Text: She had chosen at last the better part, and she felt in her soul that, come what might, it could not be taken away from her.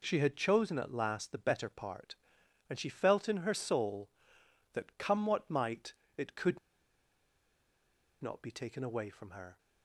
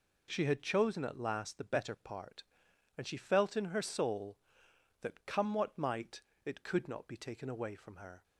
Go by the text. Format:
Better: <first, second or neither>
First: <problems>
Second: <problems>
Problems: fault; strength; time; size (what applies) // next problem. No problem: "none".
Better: second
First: pauses between "could" and "not"; strong; at 6.5 s; 1.6 s long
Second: none